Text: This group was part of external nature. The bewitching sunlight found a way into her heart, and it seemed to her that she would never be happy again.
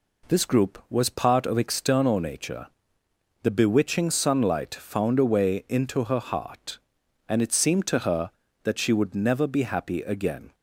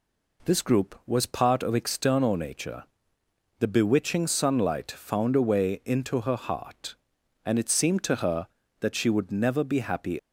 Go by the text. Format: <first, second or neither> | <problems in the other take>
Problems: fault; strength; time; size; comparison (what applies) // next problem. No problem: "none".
first | stops before "again"; at 10.1 s